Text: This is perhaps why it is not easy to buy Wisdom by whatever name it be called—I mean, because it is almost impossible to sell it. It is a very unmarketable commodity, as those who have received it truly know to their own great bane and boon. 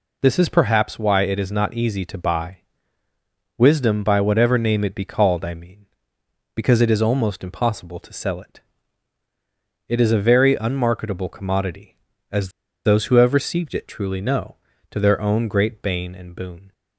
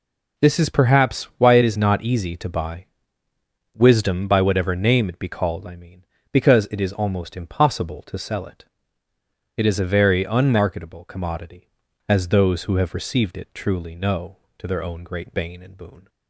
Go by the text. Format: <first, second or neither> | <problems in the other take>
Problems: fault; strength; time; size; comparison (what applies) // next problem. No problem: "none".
second | pauses between "buy" and "Wisdom"; noticeable; at 2.6 s; 0.98 s long; noticeable in the second // pauses between "as" and "those"; at 12.4 s; 0.36 s long